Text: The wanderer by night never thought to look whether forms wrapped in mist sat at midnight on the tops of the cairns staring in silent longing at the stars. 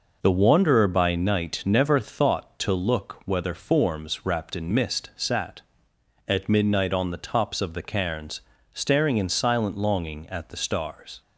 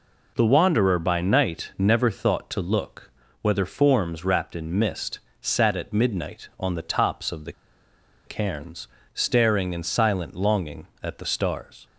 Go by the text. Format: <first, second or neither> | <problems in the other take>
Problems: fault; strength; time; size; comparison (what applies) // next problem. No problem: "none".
first | pauses between "look" and "whether"; slight; at 3.1 s; 0.30 s long // pauses between "mist" and "sat"; slight; at 5.1 s; 0.20 s long // pauses between "the" and "cairns"; noticeable; at 7.5 s; 0.73 s long // pauses between "cairns" and "staring"; slight; at 8.8 s; 0.26 s long; slight in the first